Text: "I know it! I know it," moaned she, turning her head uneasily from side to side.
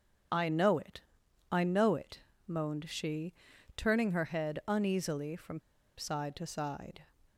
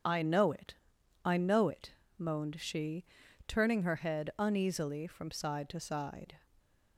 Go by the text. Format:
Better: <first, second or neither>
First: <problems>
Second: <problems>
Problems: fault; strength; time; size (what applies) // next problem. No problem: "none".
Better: second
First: starts louder than the rest; strong; until 1.8 s; 7.5 dB // pauses between "from" and "side"; at 5.5 s; 0.39 s long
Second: starts louder than the rest; strong; until 1.5 s; 7 dB